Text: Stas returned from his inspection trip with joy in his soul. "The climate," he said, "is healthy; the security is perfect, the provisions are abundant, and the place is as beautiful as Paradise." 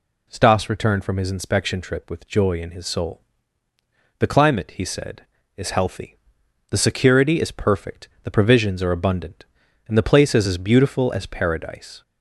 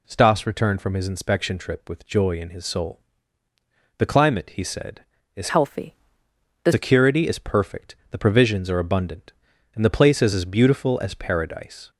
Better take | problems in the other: first | changes voice from "healthy" to "the"; from 5.5 to 6.7 s; 1.2 s long

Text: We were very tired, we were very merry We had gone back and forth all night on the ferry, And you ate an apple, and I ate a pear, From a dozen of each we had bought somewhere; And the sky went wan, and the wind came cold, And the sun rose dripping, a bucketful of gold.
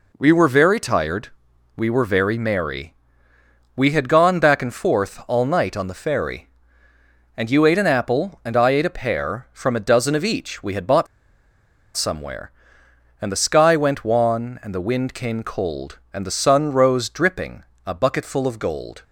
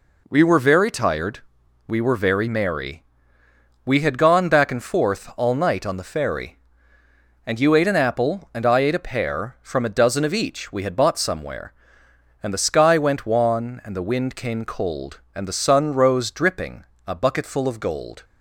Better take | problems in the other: second | pauses between "merry" and "We"; noticeable; at 2.9 s; 0.82 s long; noticeable in the second // pauses between "bought" and "somewhere"; noticeable; at 11.0 s; 0.90 s long

